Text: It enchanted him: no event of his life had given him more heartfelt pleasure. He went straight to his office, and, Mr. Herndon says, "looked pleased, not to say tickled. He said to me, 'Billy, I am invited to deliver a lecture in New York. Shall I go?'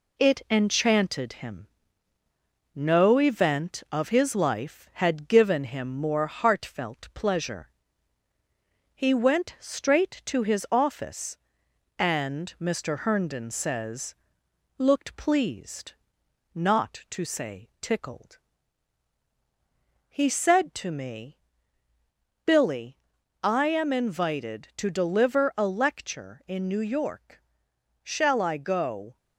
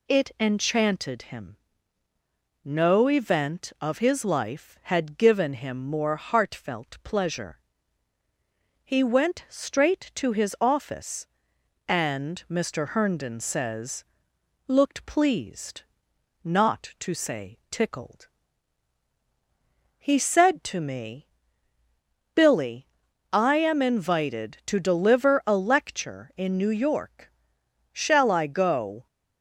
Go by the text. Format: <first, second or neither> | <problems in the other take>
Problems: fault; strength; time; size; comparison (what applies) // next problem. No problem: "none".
second | gets quieter; slight; throughout; 3.5 dB